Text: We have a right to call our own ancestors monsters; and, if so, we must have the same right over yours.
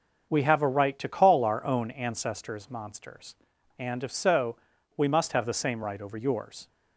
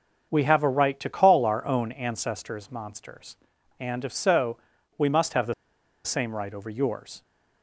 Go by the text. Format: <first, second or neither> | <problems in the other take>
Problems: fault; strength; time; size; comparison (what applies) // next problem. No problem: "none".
first | starts louder than the rest; until 1.3 s; 6.5 dB; also in the first // pauses between "the" and "same"; noticeable; at 5.5 s; 0.51 s long